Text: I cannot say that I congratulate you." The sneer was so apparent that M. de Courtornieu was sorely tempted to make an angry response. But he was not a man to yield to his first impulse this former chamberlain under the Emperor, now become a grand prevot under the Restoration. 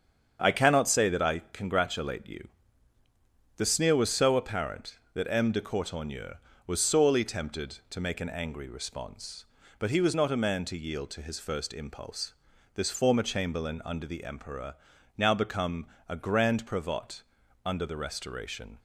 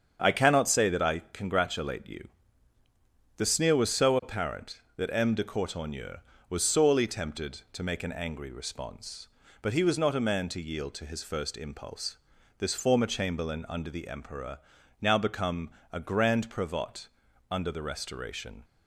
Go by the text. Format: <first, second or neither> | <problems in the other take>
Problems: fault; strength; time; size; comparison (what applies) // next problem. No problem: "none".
neither | starts louder than the rest; strong; the same in both // pauses between "impulse" and "this"; the same in both // pauses between "become" and "a"; slight; the same in both // pauses between "prevot" and "under"; the same in both